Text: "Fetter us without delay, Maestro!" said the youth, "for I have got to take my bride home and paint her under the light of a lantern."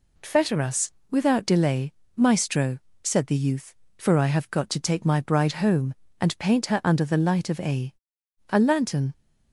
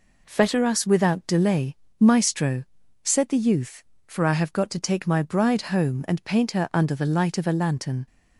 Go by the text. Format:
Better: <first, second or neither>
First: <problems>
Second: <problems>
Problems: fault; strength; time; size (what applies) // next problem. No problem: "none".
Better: second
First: pauses between "us" and "without"; slight; at 0.9 s; 0.20 s long // says "a" twice; at 8.4 s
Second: none